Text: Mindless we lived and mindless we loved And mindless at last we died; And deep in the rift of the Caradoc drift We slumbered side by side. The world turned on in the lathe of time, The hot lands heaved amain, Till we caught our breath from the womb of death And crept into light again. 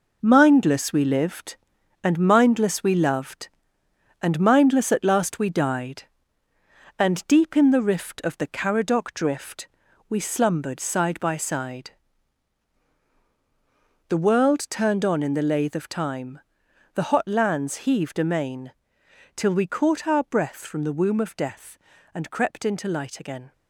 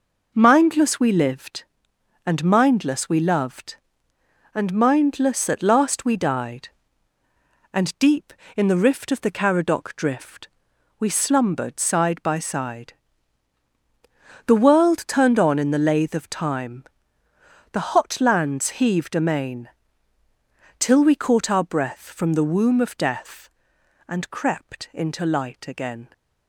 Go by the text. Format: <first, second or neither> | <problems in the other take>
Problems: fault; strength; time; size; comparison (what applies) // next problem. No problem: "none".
second | gets quieter; strong; throughout; 8 dB // pauses between "drift" and "We"; at 9.6 s; 0.44 s long; noticeable in the second